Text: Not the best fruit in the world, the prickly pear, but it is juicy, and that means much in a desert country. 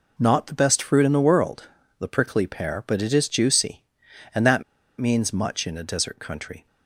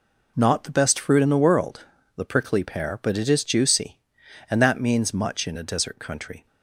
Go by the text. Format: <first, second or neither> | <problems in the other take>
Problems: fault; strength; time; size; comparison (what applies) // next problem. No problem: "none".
second | pauses between "that" and "means"; at 4.6 s; 0.36 s long